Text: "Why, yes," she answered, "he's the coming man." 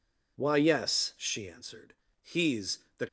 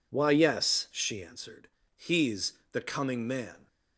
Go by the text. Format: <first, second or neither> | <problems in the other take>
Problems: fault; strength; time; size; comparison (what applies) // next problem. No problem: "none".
second | pauses between "he's" and "the"; slight; at 2.7 s; 0.18 s long; slight in the second // stops before "coming man"; at 3.0 s